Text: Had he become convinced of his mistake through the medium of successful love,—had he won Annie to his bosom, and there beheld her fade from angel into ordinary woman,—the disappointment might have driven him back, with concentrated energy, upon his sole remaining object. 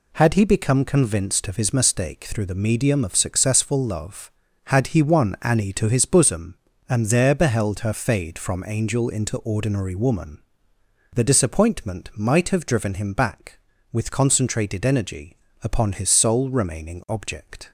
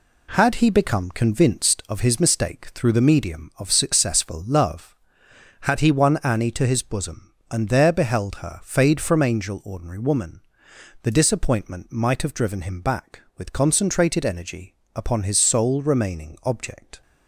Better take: first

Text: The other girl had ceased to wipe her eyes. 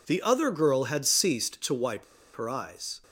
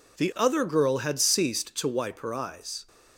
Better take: second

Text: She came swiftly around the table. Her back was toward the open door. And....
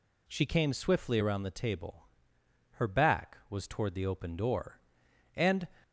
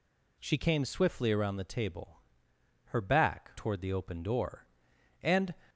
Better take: first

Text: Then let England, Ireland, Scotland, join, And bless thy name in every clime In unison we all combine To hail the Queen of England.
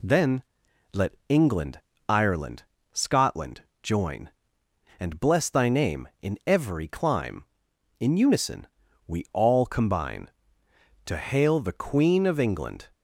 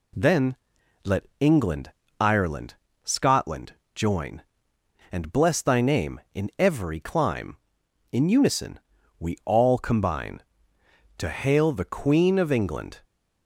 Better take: neither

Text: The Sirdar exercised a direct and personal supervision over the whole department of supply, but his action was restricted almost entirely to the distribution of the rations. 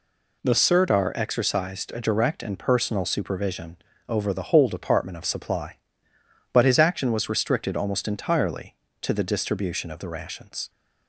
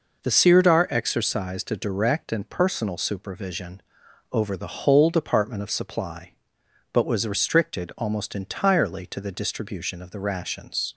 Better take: first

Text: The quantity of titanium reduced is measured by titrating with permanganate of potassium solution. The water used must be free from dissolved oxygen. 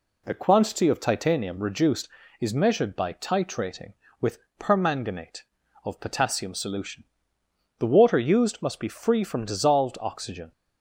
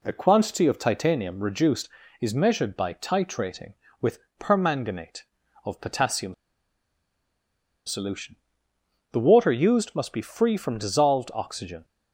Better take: first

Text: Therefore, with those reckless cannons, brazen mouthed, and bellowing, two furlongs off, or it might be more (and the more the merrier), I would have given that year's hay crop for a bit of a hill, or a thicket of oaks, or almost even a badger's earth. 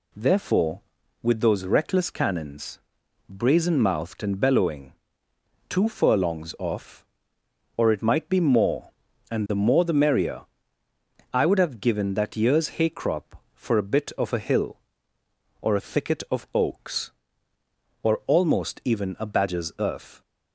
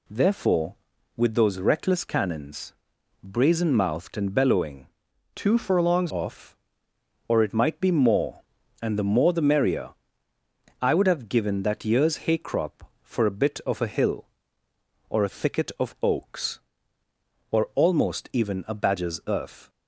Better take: first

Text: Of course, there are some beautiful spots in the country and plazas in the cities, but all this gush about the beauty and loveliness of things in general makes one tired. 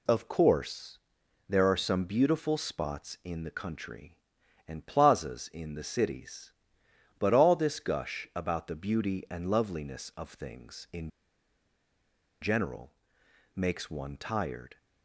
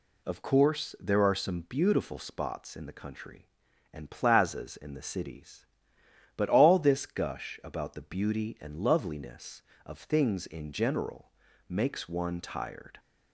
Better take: second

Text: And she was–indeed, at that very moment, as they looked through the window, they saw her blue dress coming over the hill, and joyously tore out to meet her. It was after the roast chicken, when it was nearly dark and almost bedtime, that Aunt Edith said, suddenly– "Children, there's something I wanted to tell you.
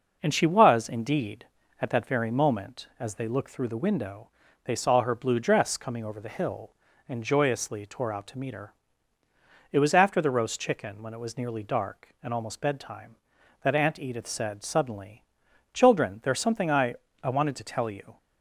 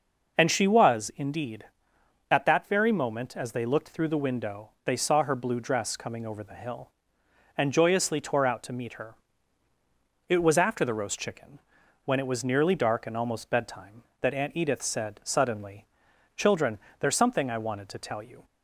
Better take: second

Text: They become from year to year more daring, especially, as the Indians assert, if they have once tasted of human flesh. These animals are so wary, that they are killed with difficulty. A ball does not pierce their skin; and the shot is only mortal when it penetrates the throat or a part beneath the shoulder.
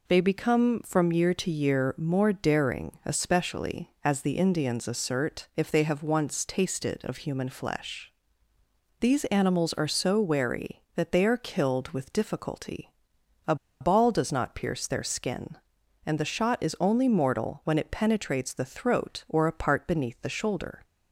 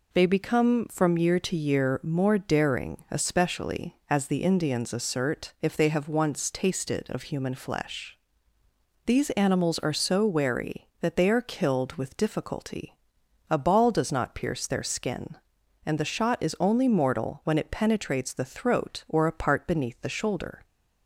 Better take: second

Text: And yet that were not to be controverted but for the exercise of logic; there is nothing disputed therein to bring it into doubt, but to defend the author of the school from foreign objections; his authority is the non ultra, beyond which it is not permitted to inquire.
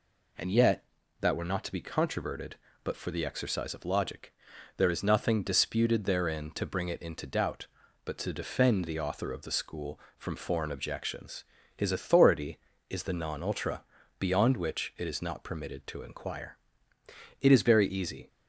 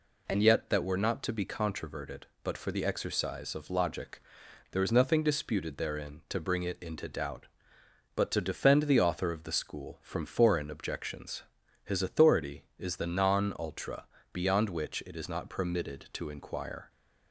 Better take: second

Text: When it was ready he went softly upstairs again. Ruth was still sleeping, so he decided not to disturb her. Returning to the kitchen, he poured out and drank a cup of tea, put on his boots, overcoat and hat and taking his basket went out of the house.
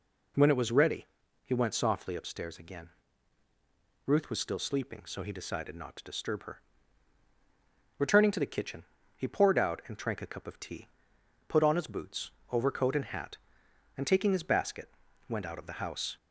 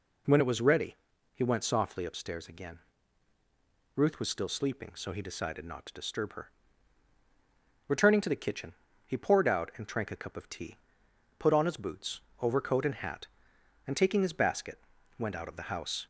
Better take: neither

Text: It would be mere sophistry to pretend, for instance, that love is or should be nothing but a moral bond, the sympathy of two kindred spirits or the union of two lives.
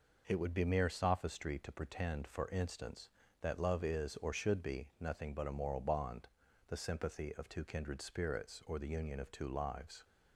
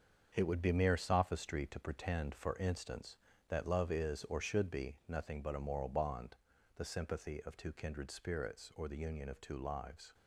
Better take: first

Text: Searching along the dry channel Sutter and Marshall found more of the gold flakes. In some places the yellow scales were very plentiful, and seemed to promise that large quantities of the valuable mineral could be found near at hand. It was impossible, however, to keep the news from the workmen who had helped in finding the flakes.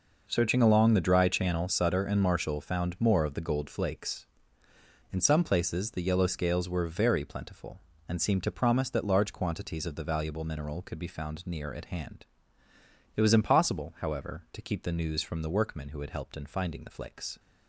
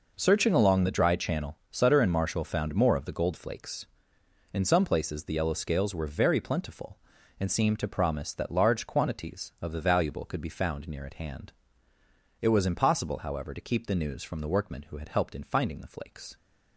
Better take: first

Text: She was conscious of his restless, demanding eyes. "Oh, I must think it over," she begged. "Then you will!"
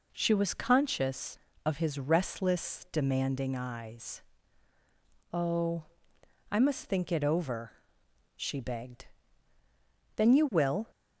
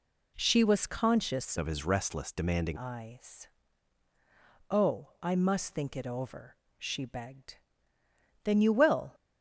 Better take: first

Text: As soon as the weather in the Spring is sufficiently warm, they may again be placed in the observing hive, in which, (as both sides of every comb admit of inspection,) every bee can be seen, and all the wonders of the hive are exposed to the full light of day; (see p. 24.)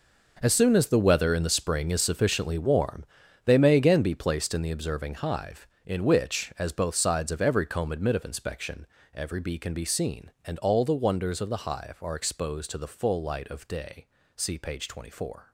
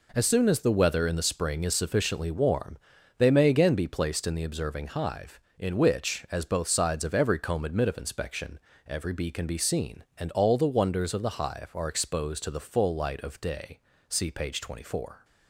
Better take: second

